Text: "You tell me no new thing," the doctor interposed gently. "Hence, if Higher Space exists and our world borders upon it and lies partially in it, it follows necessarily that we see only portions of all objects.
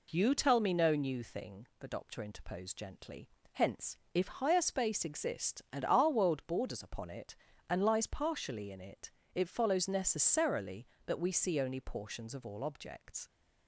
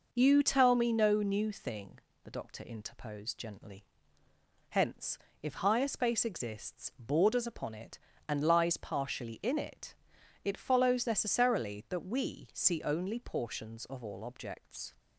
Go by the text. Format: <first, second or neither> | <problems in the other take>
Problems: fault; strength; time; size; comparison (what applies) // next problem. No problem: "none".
first | skips "and our world"; at 6.9 s